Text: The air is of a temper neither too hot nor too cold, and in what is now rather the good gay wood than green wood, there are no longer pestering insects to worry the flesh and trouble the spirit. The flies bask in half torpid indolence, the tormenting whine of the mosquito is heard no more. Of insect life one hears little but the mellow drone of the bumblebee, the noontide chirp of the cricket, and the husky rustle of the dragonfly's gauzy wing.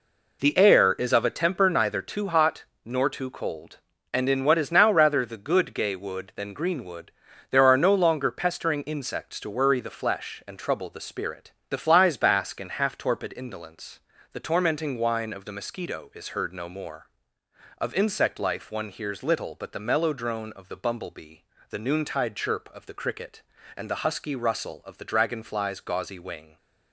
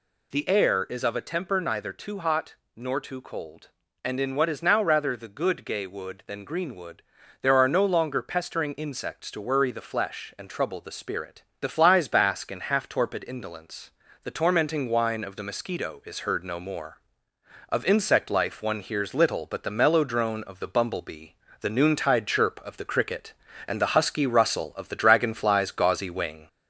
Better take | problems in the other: first | gets louder; slight; throughout; 2.5 dB // pauses between "hot" and "nor"; slight; at 2.5 s; 0.18 s long; slight in the first

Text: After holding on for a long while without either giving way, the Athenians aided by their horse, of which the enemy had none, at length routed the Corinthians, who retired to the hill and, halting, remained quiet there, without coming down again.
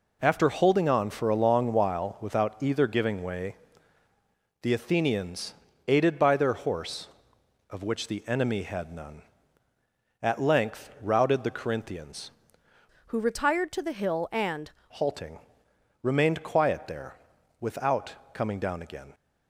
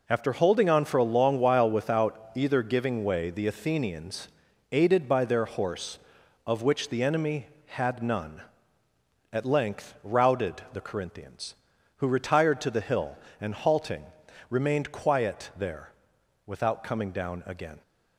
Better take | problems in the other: second | pauses between "Athenians" and "aided"; slight; at 5.5 s; 0.34 s long; also in the second // changes voice from "who" to "and"; from 13.0 to 14.7 s; 1.7 s long // pauses between "without" and "coming"; slight; at 18.1 s; 0.18 s long

